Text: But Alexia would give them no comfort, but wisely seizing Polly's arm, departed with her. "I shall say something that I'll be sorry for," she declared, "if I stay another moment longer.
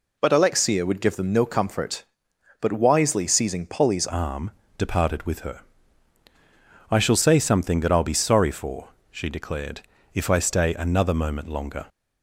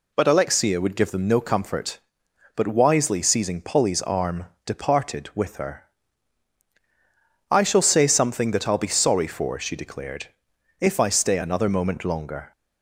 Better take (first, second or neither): second